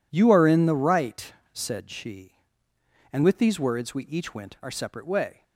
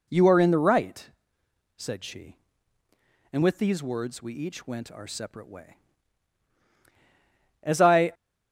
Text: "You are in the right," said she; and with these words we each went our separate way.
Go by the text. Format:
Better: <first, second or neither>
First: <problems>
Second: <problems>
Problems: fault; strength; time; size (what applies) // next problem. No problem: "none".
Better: first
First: none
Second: goes on to say "As I"; from 7.6 s on; 0.52 s long